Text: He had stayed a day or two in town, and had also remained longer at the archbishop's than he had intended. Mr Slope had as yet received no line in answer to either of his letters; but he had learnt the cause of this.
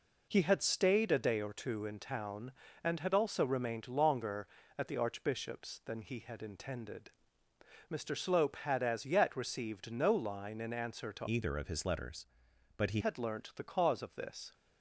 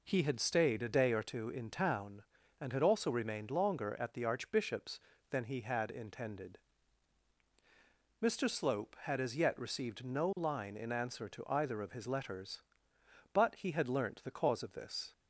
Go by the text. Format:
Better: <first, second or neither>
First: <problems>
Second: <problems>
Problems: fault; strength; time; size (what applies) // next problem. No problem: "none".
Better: second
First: changes voice from "either" to "he"; from 11.2 to 13.0 s; 1.8 s long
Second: none